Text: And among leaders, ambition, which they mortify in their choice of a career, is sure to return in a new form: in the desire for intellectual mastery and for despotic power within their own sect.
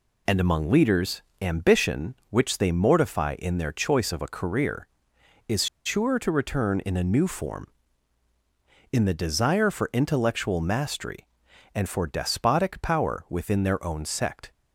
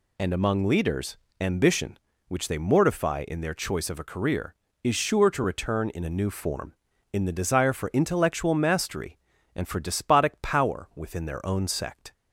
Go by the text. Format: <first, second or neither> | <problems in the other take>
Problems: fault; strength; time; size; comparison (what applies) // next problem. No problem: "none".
second | pauses between "is" and "sure"; slight; at 5.6 s; 0.19 s long